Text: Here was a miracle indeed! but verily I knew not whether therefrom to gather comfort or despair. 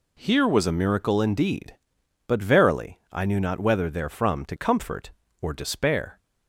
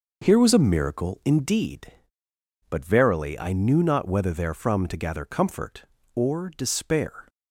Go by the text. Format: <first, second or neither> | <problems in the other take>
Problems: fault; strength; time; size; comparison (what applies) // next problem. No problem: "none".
second | skips "gather"; at 4.5 s